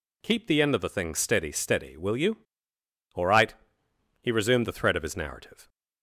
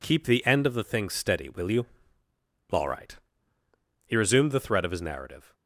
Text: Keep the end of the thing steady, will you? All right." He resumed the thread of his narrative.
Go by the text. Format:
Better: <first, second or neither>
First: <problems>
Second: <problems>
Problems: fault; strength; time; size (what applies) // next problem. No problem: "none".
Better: second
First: says "steady" twice; at 1.5 s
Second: none